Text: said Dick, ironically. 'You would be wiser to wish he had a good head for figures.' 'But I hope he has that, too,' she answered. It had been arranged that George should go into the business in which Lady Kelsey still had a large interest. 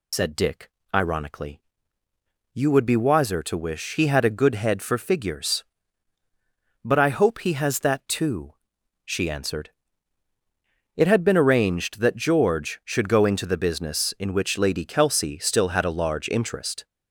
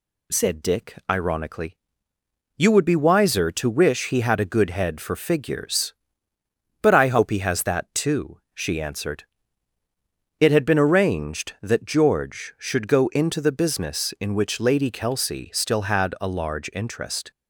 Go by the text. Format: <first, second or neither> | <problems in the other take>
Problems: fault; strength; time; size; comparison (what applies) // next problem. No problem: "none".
second | loses the start of "said"; at 0.1 s; 75 ms